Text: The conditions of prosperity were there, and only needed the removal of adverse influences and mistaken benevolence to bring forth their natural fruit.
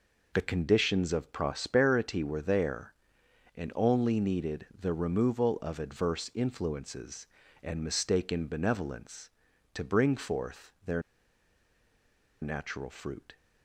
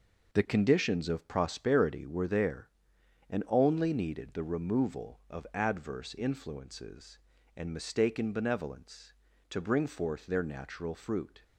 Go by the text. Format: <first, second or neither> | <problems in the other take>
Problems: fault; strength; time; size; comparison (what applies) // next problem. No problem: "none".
second | pauses between "their" and "natural"; strong; at 11.0 s; 1.4 s long